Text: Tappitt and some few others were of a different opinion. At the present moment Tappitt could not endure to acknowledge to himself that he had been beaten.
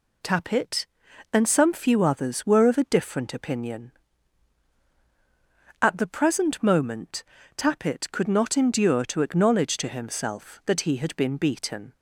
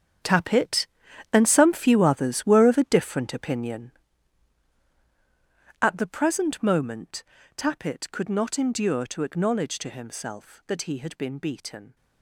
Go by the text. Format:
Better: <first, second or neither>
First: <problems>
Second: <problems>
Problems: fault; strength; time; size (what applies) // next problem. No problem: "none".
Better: first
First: pauses between "moment" and "Tappitt"; slight; at 7.2 s; 0.34 s long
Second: gets quieter; strong; throughout; 14 dB // pauses between "moment" and "Tappitt"; slight; at 7.2 s; 0.34 s long